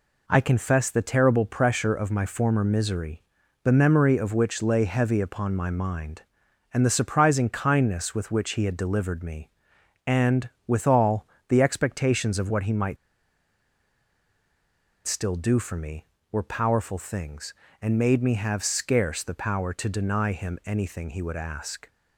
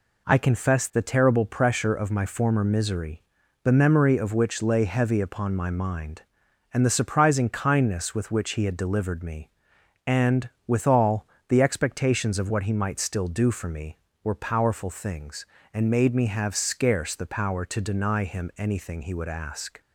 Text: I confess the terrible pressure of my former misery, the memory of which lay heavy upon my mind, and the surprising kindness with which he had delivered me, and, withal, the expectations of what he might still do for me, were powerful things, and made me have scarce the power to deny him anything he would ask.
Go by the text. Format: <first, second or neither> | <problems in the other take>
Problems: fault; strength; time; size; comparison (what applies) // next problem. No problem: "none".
second | pauses between "might" and "still"; strong; at 12.9 s; 2.0 s long